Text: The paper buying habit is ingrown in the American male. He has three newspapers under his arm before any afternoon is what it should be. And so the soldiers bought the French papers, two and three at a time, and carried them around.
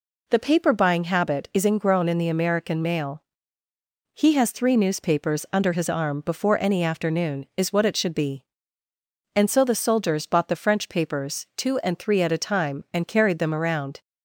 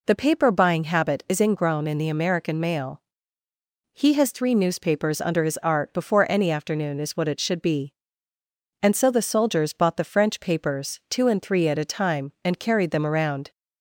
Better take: first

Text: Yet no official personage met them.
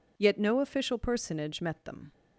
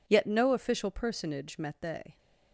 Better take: first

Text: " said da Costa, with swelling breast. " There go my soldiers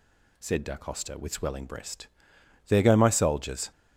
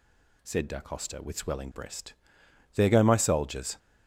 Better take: neither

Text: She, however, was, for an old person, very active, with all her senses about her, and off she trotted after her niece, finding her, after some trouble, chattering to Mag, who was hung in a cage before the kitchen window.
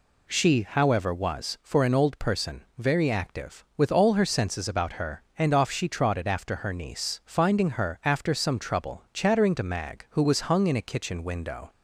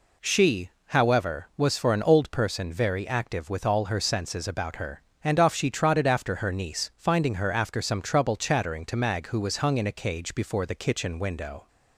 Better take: second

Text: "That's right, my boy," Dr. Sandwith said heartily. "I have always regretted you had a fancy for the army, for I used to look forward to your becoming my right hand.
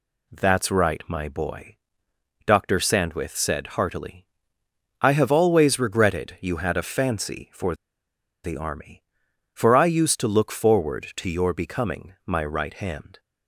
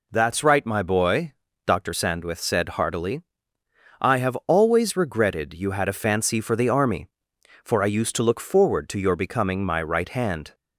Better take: second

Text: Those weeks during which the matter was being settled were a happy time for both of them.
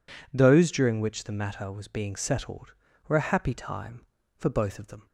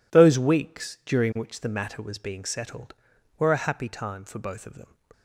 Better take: second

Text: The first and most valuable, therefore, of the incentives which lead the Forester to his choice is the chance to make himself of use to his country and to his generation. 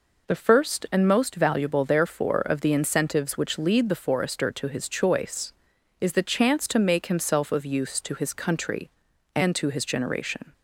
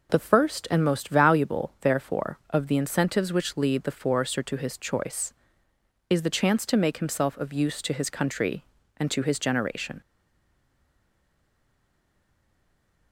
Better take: first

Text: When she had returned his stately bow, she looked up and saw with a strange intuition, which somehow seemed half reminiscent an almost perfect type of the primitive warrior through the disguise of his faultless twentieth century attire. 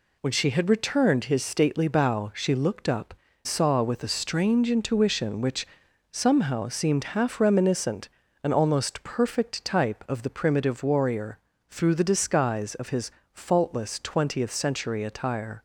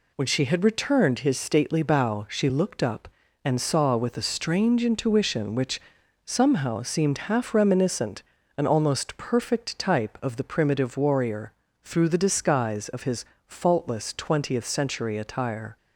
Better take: second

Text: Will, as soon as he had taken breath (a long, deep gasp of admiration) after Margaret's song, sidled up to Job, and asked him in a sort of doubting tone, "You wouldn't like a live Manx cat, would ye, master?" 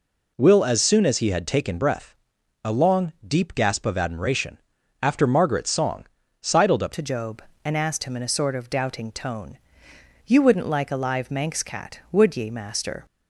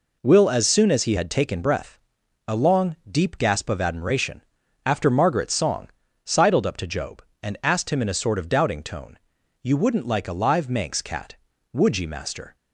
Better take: second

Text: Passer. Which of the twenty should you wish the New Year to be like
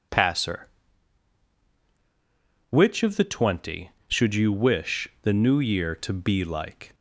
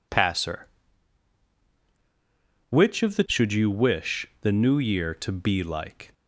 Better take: first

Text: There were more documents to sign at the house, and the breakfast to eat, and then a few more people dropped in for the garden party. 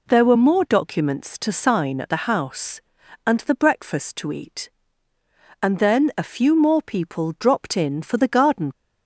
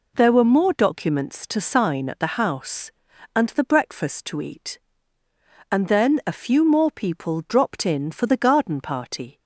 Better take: second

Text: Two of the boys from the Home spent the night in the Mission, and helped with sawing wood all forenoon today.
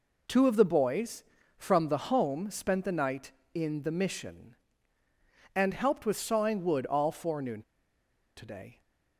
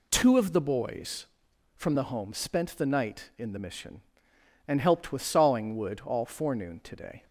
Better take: second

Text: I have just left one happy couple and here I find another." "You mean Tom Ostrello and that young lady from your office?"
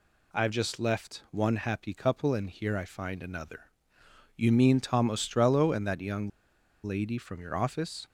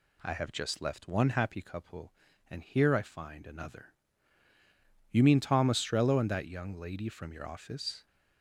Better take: second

